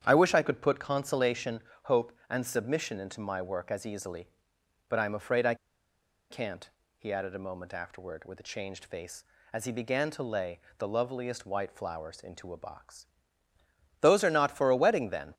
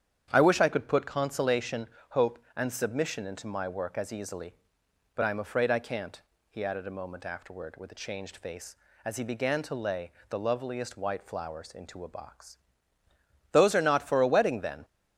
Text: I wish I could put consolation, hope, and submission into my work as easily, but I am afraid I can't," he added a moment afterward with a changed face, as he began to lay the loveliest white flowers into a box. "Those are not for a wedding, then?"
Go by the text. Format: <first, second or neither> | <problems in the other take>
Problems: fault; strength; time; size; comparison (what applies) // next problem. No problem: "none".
second | starts louder than the rest; strong; until 1.0 s; 9 dB; strong in the second // pauses between "I" and "can't"; noticeable; at 5.5 s; 0.75 s long // pauses between "lay" and "the"; slight; at 10.5 s; 0.18 s long; slight in the second